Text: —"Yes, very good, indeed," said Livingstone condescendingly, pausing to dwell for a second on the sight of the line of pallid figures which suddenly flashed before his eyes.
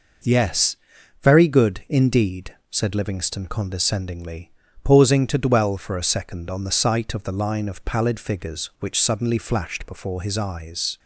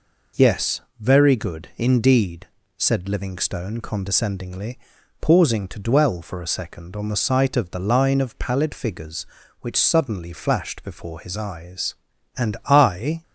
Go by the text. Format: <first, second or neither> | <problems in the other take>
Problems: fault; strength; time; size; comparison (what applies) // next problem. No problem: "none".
first | goes on to say "And I"; noticeable; from 12.3 s on; 0.86 s long